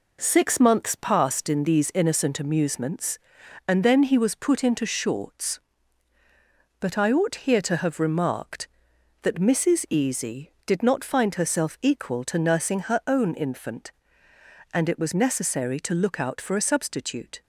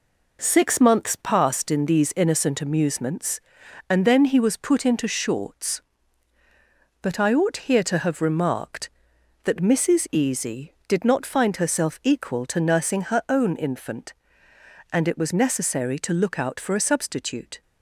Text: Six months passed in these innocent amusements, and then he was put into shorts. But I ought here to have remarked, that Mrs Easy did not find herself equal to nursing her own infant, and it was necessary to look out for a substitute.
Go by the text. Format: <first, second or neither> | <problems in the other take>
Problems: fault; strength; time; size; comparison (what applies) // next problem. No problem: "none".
neither | none